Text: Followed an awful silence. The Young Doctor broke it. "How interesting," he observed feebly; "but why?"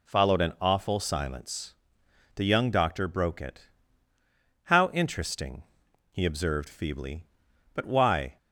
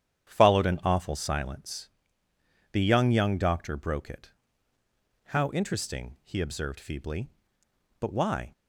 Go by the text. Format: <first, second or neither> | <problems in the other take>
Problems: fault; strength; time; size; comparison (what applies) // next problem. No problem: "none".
first | starts louder than the rest; strong; until 1.3 s; 9.5 dB // says "Young" twice; at 3.0 s